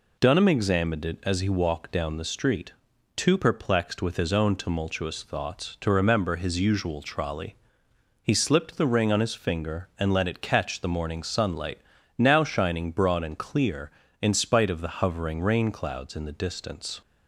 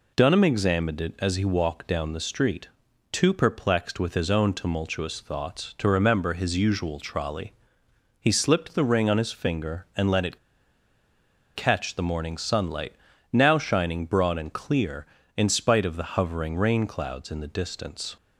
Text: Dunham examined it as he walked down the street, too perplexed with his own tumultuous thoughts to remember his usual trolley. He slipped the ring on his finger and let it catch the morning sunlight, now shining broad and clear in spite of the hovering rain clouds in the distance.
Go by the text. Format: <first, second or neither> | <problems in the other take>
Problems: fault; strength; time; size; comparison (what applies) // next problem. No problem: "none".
first | pauses between "it" and "catch"; at 10.3 s; 1.1 s long